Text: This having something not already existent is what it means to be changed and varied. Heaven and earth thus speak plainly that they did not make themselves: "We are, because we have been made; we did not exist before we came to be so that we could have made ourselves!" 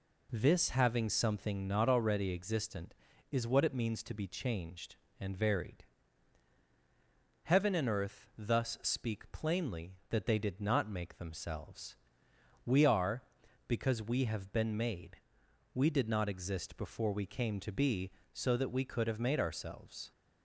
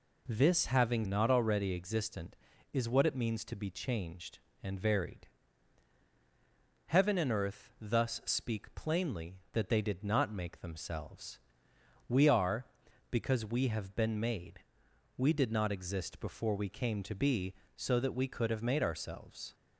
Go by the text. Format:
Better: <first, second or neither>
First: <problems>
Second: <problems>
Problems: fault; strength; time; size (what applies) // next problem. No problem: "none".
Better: first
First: none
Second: skips "something"; at 1.0 s